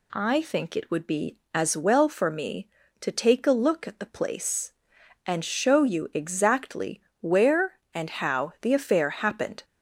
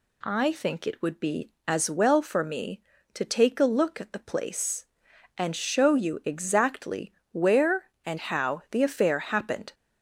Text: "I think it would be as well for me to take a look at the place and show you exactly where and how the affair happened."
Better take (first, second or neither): neither